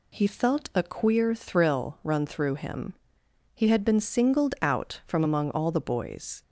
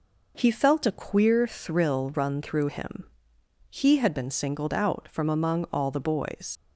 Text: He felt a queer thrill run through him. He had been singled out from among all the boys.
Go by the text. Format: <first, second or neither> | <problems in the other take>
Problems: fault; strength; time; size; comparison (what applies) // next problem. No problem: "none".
first | leaves "boys" unfinished; at 6.5 s; 80 ms